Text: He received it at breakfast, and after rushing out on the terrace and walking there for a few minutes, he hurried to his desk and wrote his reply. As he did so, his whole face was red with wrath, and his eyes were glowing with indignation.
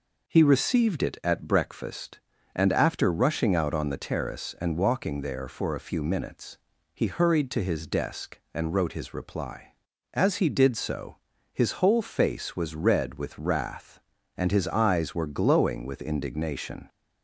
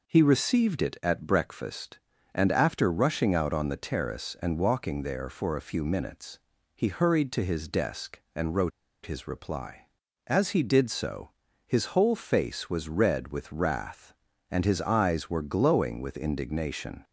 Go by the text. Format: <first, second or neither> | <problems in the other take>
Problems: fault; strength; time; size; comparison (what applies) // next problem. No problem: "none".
first | pauses between "wrote" and "his"; slight; at 8.7 s; 0.34 s long